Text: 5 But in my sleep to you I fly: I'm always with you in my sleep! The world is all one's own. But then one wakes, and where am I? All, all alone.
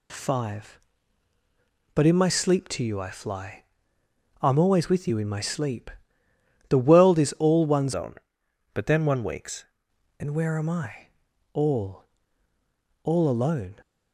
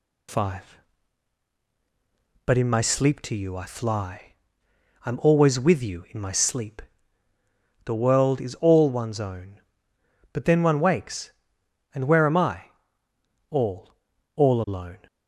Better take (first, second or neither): second